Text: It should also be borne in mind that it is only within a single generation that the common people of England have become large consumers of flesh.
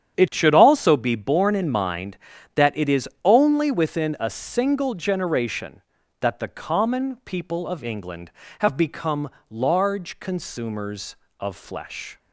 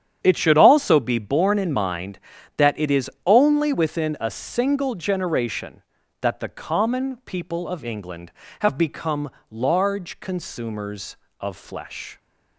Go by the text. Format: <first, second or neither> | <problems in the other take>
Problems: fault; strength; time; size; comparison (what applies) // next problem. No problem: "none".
neither | starts louder than the rest; strong; the same in both // pauses between "is" and "only"; slight; the same in both // pauses between "become" and "large"; slight; the same in both